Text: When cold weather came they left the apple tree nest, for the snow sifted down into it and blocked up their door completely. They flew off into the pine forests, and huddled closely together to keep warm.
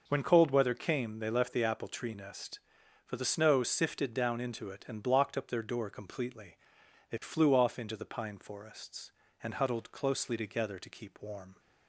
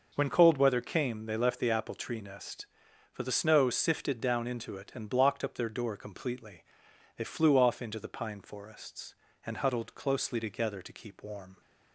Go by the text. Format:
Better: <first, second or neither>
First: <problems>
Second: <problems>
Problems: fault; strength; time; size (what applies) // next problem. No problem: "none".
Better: neither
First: none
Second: none